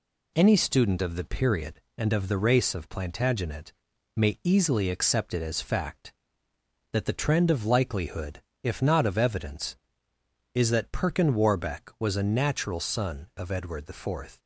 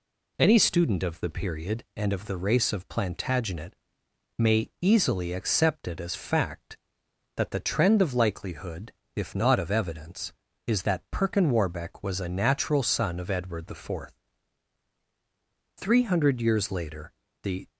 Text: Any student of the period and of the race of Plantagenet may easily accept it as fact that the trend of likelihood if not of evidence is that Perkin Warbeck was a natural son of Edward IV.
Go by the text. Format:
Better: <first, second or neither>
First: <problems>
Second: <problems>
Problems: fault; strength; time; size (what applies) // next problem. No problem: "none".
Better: first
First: pauses between "Plantagenet" and "may"; at 3.7 s; 0.44 s long // pauses between "likelihood" and "if"; slight; at 8.4 s; 0.22 s long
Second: pauses between "Plantagenet" and "may"; noticeable; at 3.7 s; 0.64 s long // pauses between "likelihood" and "if"; slight; at 8.9 s; 0.24 s long // goes on to say "Three hundred years later the"; strong; from 15.7 s on; 1.9 s long